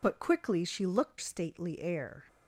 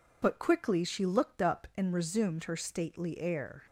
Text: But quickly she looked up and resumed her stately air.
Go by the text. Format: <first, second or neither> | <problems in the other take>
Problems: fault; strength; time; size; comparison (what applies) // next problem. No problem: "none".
second | skips "up and resumed her"; at 1.1 s